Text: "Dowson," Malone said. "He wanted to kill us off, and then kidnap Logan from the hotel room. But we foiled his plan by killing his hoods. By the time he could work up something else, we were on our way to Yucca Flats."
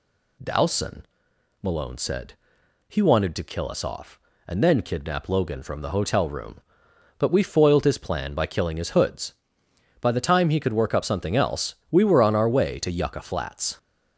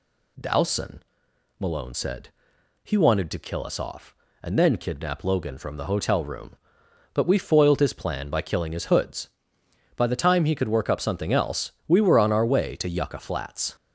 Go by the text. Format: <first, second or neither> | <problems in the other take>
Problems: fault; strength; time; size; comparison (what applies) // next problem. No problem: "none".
neither | none